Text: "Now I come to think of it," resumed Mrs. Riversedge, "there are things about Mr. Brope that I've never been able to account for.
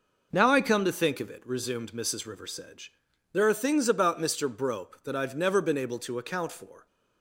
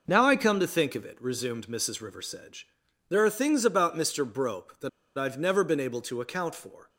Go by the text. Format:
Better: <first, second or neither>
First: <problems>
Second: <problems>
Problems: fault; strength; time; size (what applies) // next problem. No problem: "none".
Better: first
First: none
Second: pauses between "that" and "I've"; slight; at 4.8 s; 0.27 s long